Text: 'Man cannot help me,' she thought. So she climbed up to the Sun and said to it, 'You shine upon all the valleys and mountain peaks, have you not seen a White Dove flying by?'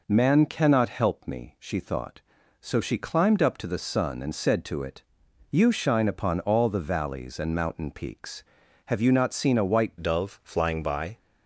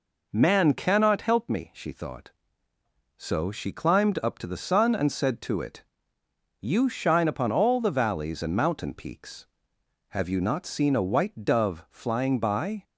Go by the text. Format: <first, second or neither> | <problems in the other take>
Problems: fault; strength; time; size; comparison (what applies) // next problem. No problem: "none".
second | changes voice at "Dove"; from 10.0 s on; 1.1 s long